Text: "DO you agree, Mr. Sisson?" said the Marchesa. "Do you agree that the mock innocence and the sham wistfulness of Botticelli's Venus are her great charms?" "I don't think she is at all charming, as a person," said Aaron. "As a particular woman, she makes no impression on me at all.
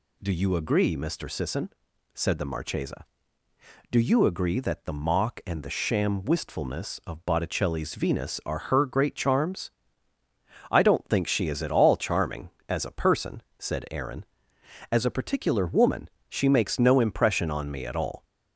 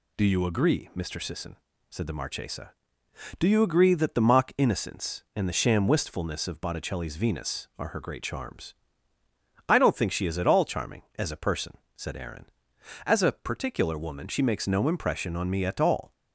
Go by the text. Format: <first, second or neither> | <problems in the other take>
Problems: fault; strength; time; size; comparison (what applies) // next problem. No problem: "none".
second | skips "innocence"; at 5.4 s